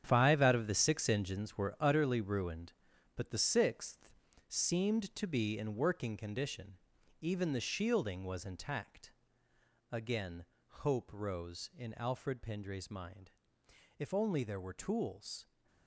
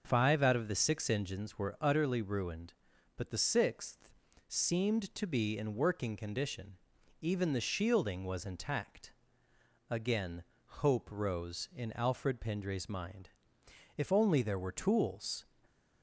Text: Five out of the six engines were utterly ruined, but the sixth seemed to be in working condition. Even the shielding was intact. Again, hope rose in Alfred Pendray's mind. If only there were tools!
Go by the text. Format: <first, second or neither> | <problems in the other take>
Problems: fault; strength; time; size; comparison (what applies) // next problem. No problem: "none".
second | gets quieter; strong; throughout; 10 dB // starts louder than the rest; strong; until 1.0 s; 8.5 dB; noticeable in the second // pauses between "sixth" and "seemed"; slight; at 4.1 s; 0.34 s long; slight in the second